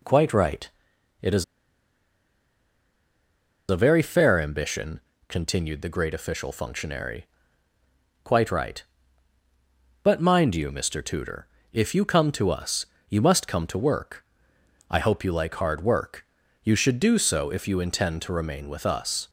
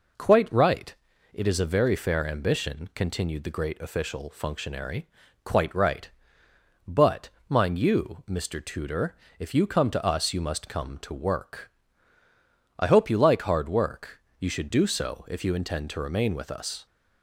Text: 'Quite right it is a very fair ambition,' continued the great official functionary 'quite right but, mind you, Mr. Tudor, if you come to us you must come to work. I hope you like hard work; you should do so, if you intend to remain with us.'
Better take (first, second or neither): second